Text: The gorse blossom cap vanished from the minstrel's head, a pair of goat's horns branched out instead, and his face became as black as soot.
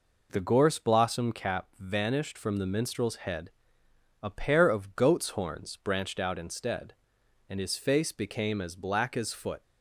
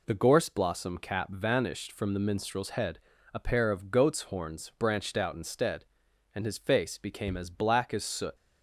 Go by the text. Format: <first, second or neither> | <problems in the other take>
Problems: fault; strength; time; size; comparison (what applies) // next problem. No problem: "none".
second | says "foot" for "soot"; at 9.3 s